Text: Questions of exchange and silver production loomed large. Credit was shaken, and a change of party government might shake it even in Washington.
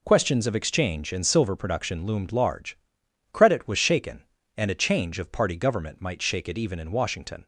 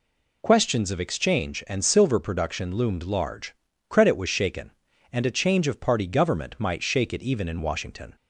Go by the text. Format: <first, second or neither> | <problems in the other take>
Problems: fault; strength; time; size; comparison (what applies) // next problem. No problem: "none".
neither | none